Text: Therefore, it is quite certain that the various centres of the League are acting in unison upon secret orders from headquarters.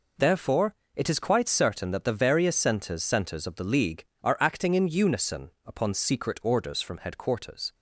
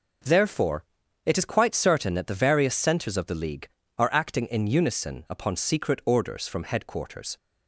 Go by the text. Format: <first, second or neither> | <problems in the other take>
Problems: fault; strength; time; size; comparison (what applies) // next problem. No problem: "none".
second | says "centres" twice; at 3.0 s // pauses between "unison" and "upon"; slight; at 5.5 s; 0.16 s long